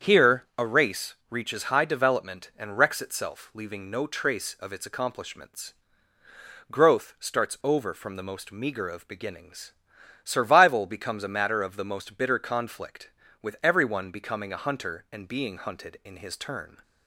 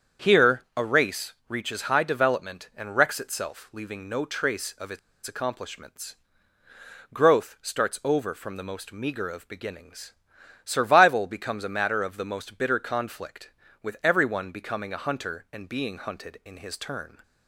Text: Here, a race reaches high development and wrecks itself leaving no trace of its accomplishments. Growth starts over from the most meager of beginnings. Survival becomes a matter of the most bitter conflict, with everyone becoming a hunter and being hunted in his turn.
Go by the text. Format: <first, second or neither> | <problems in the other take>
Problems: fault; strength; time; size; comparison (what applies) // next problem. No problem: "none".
first | starts louder than the rest; strong; until 1.3 s; 7.5 dB; strong in the first // pauses between "race" and "reaches"; slight; at 1.3 s; 0.16 s long; slight in the first // pauses between "its" and "accomplishments"; slight; at 4.9 s; 0.26 s long